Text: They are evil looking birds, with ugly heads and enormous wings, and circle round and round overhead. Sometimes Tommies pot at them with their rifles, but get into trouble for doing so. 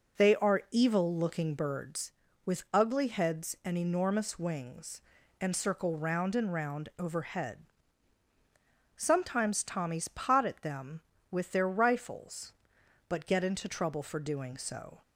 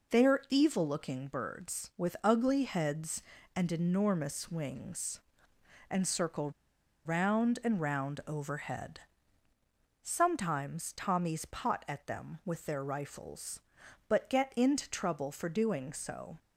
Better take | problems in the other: first | pauses between "circle" and "round"; noticeable; at 6.4 s; 0.55 s long

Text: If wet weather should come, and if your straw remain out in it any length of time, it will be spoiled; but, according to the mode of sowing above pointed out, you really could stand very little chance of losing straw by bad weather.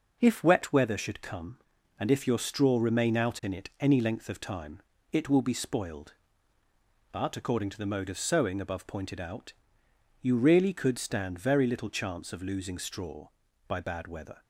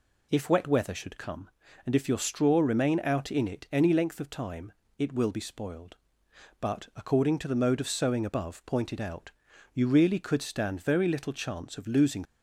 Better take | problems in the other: first | stops before "straw by bad weather"; at 12.2 s

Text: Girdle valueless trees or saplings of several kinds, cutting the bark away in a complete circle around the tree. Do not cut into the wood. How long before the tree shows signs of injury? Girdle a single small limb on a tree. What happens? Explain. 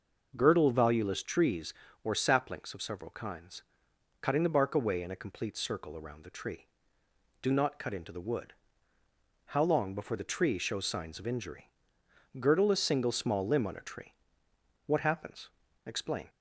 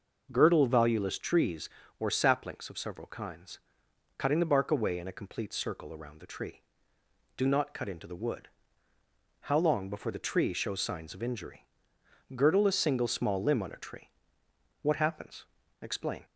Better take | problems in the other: neither | none

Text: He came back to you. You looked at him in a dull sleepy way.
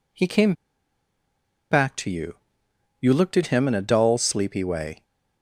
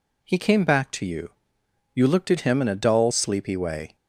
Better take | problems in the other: second | pauses between "came" and "back"; at 0.5 s; 1.1 s long

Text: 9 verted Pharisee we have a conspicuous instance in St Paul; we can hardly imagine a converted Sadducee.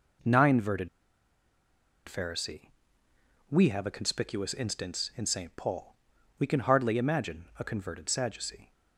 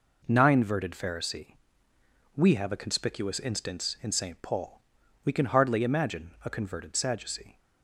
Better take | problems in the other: second | pauses between "verted" and "Pharisee"; at 0.8 s; 1.1 s long // pauses between "Pharisee" and "we"; noticeable; at 2.6 s; 0.80 s long; noticeable in the second

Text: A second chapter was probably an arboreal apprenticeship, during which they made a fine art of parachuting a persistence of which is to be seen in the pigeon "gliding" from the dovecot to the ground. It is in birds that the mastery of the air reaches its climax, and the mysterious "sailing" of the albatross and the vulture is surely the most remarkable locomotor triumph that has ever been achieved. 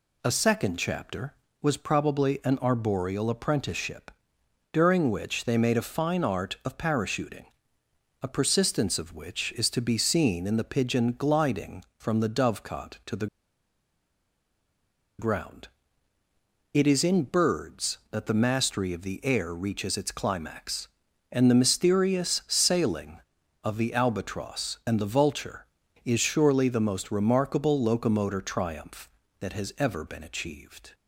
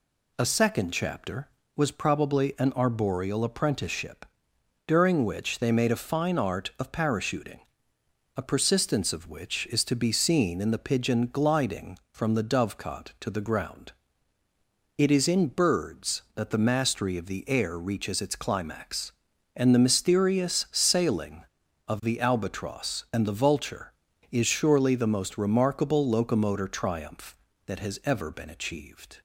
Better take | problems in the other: second | pauses between "parachuting" and "a"; noticeable; at 7.4 s; 0.76 s long; noticeable in the second // pauses between "the" and "ground"; strong; at 13.2 s; 1.9 s long

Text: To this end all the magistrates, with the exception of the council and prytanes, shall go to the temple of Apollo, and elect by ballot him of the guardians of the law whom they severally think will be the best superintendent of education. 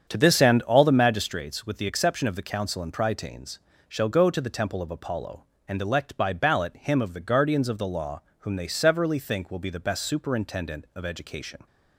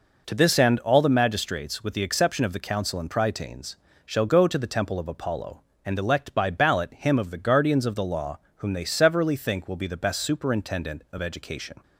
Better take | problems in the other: second | starts louder than the rest; strong; until 1.3 s; 8 dB // pauses between "law" and "whom"; slight; at 8.2 s; 0.18 s long; slight in the second

